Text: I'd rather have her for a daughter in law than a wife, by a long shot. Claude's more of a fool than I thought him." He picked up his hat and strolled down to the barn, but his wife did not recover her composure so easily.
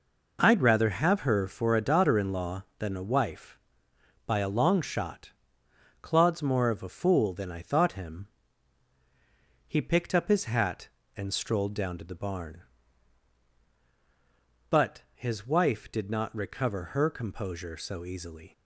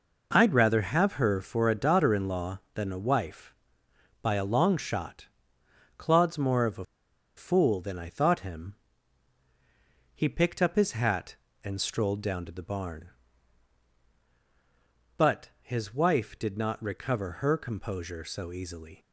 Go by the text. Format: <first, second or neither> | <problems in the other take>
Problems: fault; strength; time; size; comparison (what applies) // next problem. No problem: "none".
first | pauses between "a" and "fool"; noticeable; at 6.8 s; 0.52 s long